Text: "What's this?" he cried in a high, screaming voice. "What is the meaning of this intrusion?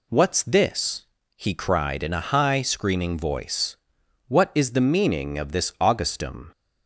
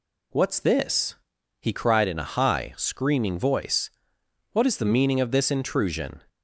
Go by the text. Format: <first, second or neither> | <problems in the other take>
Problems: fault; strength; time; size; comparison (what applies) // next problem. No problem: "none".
second | says "augustum" for "intrusion"; at 5.8 s